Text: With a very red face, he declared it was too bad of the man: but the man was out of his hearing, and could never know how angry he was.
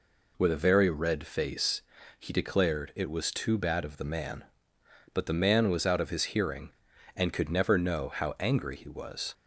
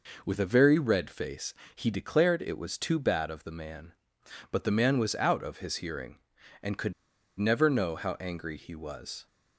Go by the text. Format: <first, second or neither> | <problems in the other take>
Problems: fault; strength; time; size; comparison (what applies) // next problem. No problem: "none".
first | pauses between "could" and "never"; at 6.9 s; 0.45 s long